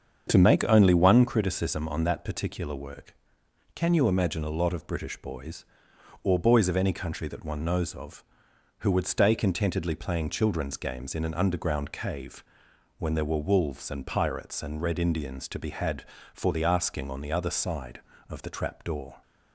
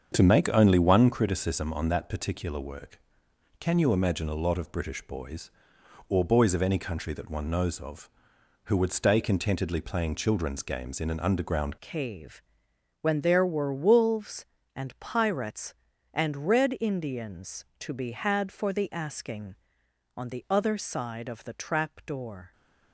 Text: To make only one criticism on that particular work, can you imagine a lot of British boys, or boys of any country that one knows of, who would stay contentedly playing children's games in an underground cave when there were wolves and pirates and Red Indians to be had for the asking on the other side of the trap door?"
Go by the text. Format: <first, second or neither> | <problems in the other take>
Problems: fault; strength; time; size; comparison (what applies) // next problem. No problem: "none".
first | starts louder than the rest; strong; until 1.1 s; 7 dB; strong in the first // changes voice at "cave"; from 11.7 s on; 10.8 s long // pauses between "cave" and "when"; noticeable; at 12.3 s; 0.62 s long; noticeable in the first